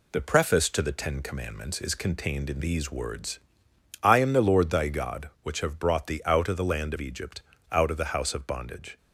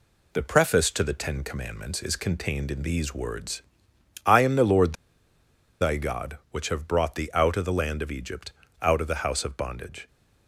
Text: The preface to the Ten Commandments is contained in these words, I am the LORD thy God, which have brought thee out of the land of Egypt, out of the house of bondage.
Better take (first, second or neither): first